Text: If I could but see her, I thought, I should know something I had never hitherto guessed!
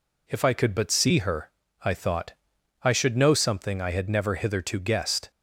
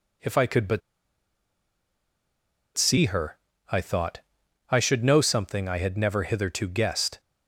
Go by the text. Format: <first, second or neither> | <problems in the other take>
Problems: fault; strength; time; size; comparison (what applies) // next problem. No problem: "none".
first | pauses between "but" and "see"; strong; at 0.8 s; 1.9 s long